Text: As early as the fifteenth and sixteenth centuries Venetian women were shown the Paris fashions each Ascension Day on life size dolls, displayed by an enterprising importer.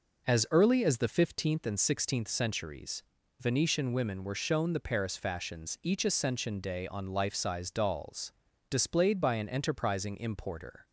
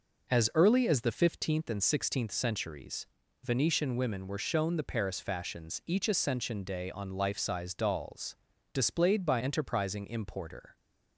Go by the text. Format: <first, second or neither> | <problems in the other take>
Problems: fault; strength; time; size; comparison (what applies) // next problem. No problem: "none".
first | pauses between "centuries" and "Venetian"; slight; at 3.0 s; 0.36 s long; slight in the first // skips "an"; at 9.3 s